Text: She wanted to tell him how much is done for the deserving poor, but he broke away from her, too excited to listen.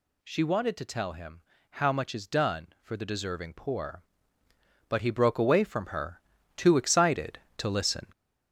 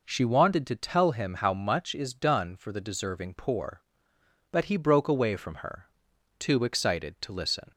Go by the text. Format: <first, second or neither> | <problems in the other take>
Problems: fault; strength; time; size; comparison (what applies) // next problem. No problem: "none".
second | gets louder; noticeable; throughout; 5 dB // pauses between "him" and "how"; slight; at 1.4 s; 0.30 s long